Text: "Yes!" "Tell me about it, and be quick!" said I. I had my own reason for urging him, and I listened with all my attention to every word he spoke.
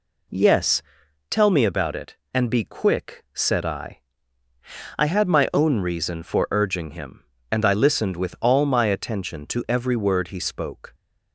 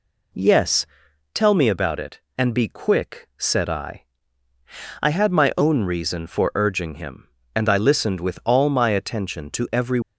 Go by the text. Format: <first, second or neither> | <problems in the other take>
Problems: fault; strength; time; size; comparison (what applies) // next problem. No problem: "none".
first | stops before "word he spoke"; at 10.0 s